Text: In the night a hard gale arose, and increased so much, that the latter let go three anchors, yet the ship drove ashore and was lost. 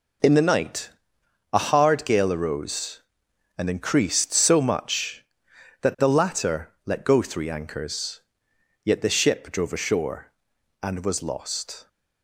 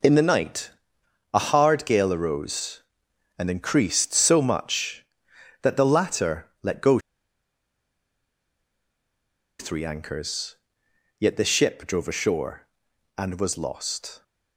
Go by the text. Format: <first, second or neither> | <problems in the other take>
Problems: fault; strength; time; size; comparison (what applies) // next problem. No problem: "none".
first | pauses between "night" and "a"; noticeable; at 0.7 s; 0.60 s long; noticeable in the first // pauses between "latter" and "let"; slight; at 6.4 s; 0.16 s long; slight in the first // pauses between "go" and "three"; strong; at 6.9 s; 2.6 s long